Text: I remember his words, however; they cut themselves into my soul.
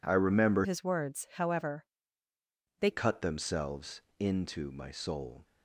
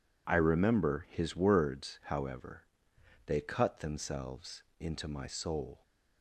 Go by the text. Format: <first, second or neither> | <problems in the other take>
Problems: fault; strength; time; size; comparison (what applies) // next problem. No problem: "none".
second | changes voice from "his" to "they"; from 0.6 to 2.8 s; 2.2 s long // pauses between "themselves" and "into"; slight; at 4.0 s; 0.18 s long; slight in the second